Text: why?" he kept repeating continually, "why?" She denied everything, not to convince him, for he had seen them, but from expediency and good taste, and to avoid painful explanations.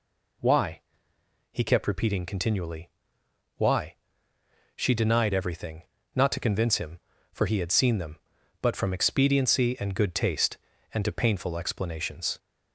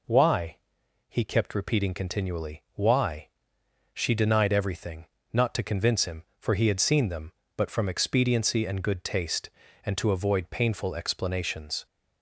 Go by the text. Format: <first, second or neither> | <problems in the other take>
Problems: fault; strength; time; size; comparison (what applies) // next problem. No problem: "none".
second | skips "avoid"; at 11.1 s